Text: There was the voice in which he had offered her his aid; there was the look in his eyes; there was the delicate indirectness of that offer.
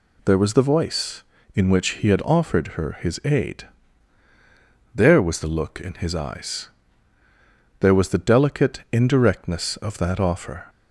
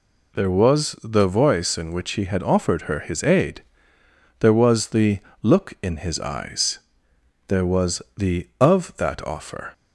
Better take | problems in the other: first | pauses between "the" and "look"; slight; at 5.1 s; 0.24 s long // pauses between "was" and "the"; slight; at 8.0 s; 0.16 s long // skips "delicate indirectness"; at 8.5 s

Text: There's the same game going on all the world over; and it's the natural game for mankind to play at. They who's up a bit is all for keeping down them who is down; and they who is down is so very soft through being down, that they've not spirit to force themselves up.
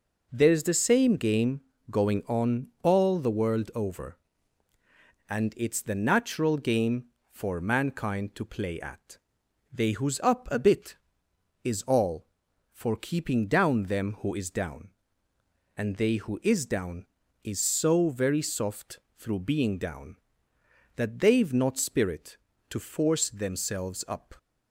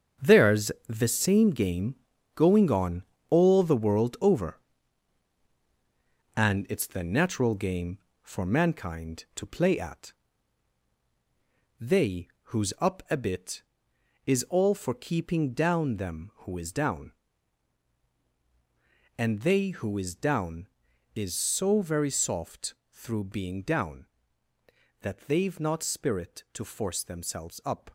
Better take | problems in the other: first | gets quieter; strong; throughout; 9.5 dB // pauses between "There's" and "the"; slight; at 0.7 s; 0.16 s long // pauses between "game" and "going"; at 1.9 s; 0.40 s long; slight in the first // pauses between "on" and "all"; slight; at 3.0 s; 0.26 s long // pauses between "They" and "who's"; slight; at 12.2 s; 0.24 s long // pauses between "soft" and "through"; slight; at 22.7 s; 0.16 s long; slight in the first

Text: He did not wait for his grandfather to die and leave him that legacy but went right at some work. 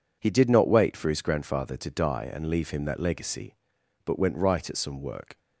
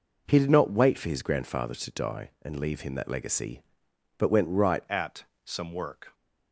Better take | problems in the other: first | changes voice at "at"; from 4.8 s on; 1.3 s long // pauses between "at" and "some"; slight; at 5.2 s; 0.20 s long

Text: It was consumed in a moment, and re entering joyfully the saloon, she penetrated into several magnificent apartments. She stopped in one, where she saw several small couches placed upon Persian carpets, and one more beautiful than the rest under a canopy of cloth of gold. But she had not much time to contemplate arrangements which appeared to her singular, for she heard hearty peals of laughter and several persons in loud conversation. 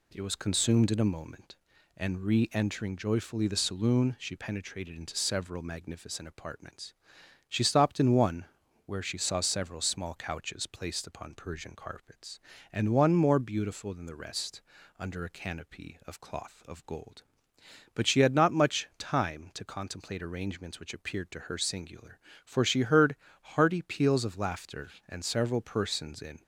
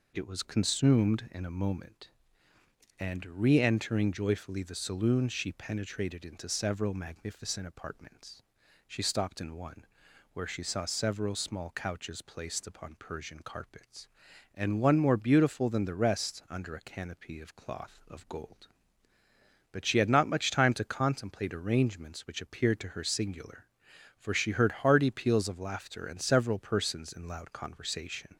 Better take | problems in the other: second | pauses between "rest" and "under"; at 14.6 s; 0.38 s long // pauses between "heard" and "hearty"; slight; at 23.1 s; 0.26 s long // stops before "loud conversation"; at 26.4 s

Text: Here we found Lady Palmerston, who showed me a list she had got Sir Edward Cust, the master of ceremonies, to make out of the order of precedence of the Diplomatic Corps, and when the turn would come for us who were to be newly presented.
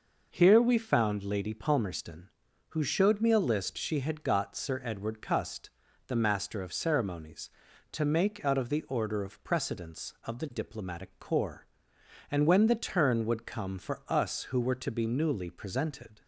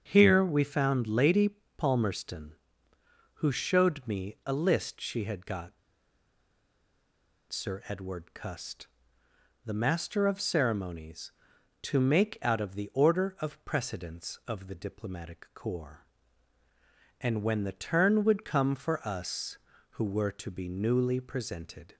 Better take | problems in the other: first | starts louder than the rest; until 1.0 s; 7 dB // pauses between "Lady" and "Palmerston"; slight; at 1.4 s; 0.28 s long // pauses between "got" and "Sir"; strong; at 5.7 s; 1.7 s long

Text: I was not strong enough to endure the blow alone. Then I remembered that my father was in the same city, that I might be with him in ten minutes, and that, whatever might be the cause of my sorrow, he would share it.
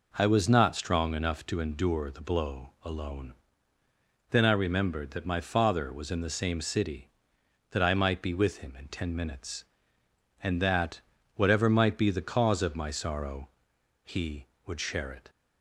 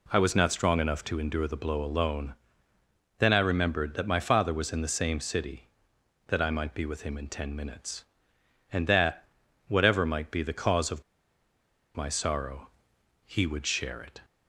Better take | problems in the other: first | pauses between "of" and "my"; noticeable; at 11.0 s; 0.93 s long

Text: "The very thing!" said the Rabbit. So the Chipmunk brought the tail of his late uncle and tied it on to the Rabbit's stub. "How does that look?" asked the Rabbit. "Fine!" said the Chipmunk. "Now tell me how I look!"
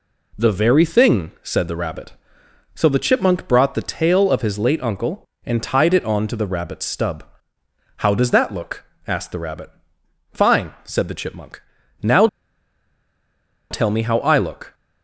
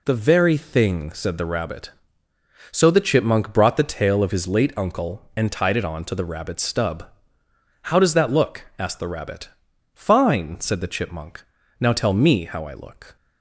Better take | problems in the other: second | pauses between "Now" and "tell"; strong; at 12.2 s; 1.4 s long

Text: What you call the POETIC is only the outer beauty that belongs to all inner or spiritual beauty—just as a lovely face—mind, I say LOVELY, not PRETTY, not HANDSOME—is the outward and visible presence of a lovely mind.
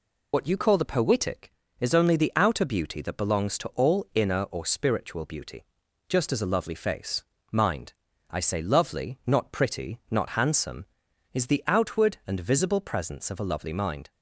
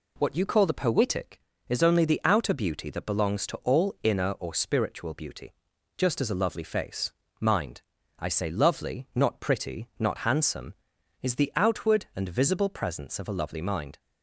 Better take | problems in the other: second | loses the start of "What"; at 0.3 s; 65 ms

